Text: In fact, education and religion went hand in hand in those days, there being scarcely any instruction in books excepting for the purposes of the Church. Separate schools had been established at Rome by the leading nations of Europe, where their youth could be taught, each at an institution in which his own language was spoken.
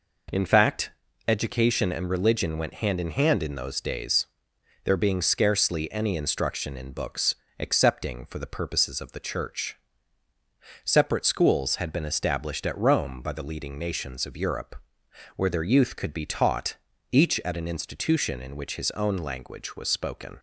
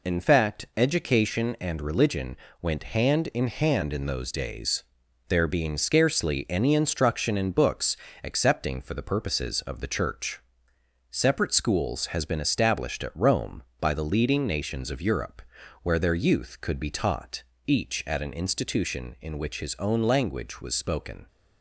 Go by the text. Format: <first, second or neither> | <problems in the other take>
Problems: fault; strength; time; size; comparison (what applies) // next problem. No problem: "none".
first | pauses between "religion" and "went"; slight; at 2.3 s; 0.24 s long // pauses between "books" and "excepting"; slight; at 7.9 s; 0.26 s long; slight in the first // says "has" for "had"; at 12.0 s